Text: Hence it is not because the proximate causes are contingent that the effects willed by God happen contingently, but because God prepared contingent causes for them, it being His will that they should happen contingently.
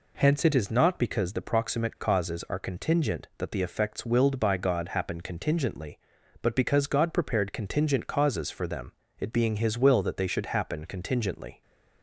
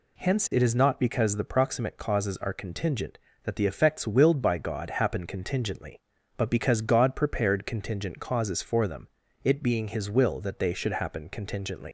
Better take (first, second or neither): first